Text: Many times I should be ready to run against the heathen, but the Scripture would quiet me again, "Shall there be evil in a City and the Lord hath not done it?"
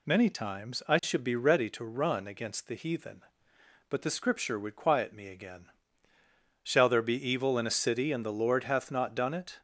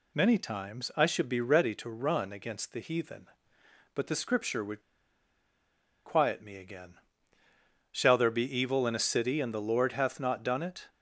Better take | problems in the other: first | pauses between "would" and "quiet"; at 4.8 s; 1.2 s long

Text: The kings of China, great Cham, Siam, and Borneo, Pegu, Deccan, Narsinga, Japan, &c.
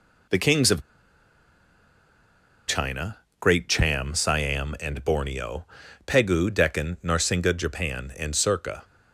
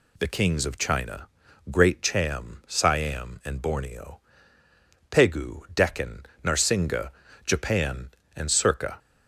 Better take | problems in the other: second | pauses between "of" and "China"; strong; at 0.8 s; 1.8 s long

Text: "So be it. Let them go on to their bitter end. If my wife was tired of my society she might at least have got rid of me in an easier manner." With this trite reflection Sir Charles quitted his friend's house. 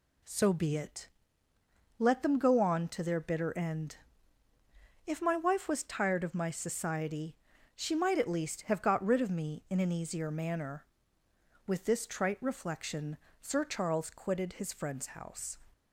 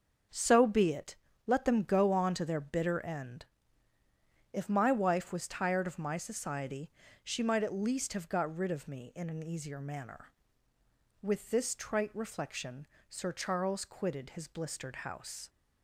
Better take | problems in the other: first | starts louder than the rest; until 1.6 s; 6.5 dB // pauses between "society" and "she"; slight; at 6.8 s; 0.34 s long; also in the first // pauses between "reflection" and "Sir"; slight; at 12.8 s; 0.20 s long; slight in the first // says "blistered" for "friend's"; at 14.4 s

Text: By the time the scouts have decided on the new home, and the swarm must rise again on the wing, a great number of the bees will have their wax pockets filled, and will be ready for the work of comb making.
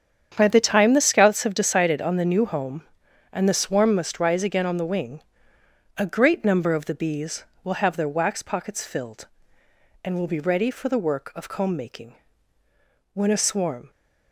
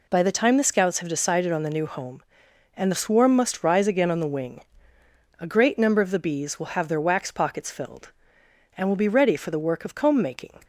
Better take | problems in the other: second | starts louder than the rest; strong; until 1.3 s; 8 dB // goes on to say "When a swarm"; noticeable; from 13.1 s on; 0.76 s long

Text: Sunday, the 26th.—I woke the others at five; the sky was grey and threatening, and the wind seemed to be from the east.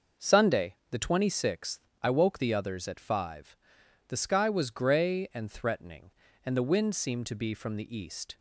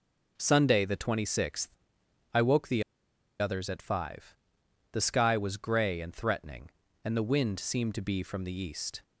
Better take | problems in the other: first | pauses between "the" and "others"; noticeable; at 2.8 s; 0.57 s long

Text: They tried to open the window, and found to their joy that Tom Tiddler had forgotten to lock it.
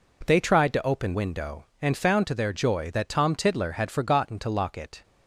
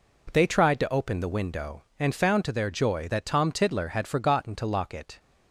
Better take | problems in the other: second | skips "the"; at 1.1 s

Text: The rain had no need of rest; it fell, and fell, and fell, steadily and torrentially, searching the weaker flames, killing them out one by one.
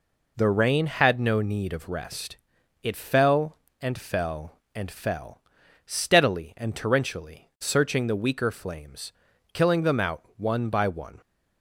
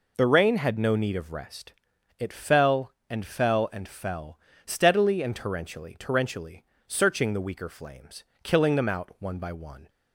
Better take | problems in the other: first | says "torrentially" twice; at 5.9 s

